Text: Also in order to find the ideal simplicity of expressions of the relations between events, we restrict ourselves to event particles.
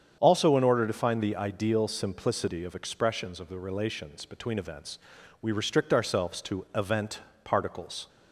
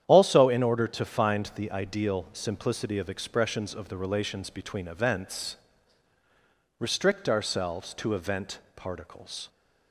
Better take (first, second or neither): first